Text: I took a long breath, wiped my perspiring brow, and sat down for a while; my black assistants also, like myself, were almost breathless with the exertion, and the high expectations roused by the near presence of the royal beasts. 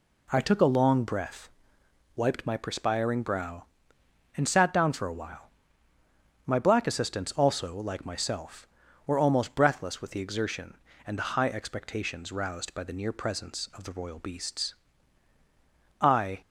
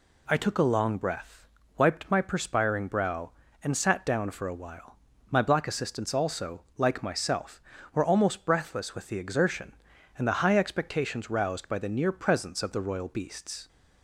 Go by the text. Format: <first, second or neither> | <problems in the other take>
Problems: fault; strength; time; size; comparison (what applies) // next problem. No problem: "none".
second | goes on to say "I"; slight; from 15.9 s on; 0.42 s long